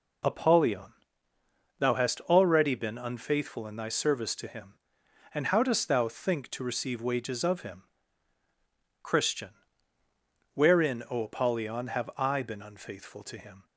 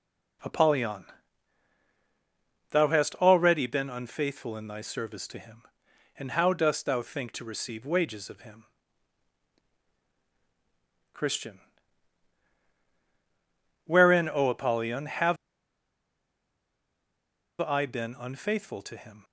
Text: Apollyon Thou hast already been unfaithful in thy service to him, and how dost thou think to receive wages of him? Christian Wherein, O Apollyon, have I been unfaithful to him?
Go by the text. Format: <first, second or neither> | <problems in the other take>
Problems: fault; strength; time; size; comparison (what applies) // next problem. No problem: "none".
first | pauses between "Apollyon" and "Thou"; strong; at 1.0 s; 1.6 s long; noticeable in the first // pauses between "Christian" and "Wherein"; strong; at 11.5 s; 2.2 s long; also in the first // pauses between "have" and "I"; strong; at 15.3 s; 2.2 s long